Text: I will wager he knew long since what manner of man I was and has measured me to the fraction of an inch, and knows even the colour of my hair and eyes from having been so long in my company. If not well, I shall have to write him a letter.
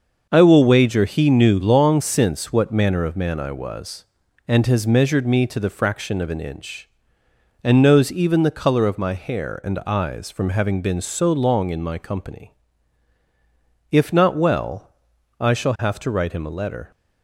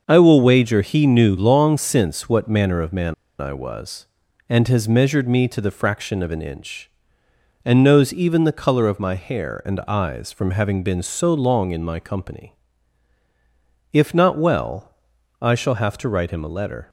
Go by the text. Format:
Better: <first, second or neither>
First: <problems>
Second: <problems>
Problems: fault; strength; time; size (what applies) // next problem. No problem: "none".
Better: first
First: starts louder than the rest; until 1.3 s; 6.5 dB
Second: starts louder than the rest; until 1.0 s; 6.5 dB // pauses between "man" and "I"; slight; at 3.1 s; 0.26 s long